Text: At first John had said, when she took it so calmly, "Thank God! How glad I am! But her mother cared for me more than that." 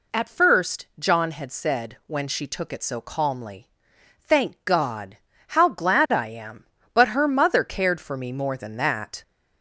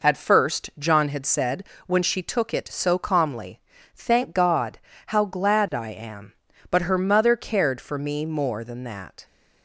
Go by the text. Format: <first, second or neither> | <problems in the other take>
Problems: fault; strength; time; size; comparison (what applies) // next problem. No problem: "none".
second | gets louder; slight; throughout; 2 dB